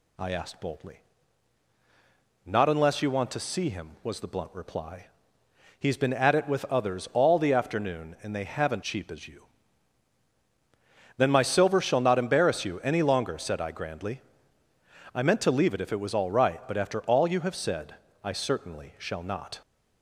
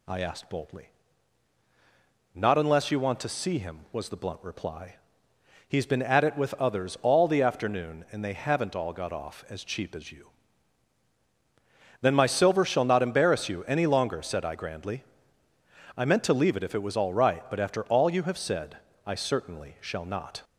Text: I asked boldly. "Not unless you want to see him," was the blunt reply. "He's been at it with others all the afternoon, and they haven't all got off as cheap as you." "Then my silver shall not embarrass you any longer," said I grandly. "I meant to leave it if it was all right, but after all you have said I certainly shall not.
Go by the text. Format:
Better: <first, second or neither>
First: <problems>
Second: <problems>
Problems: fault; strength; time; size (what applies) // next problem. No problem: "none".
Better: second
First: skips "all got off as"; at 8.8 s // pauses between "said" and "I"; slight; at 17.9 s; 0.28 s long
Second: pauses between "said" and "I"; slight; at 18.7 s; 0.28 s long